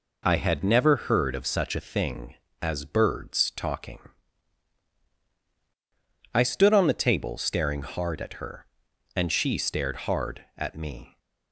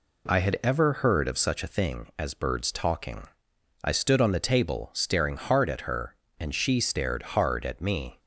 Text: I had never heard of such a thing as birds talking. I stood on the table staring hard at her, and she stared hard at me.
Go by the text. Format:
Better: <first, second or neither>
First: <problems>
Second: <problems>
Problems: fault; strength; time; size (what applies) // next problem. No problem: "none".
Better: first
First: none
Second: says "ever" for "never"; at 0.6 s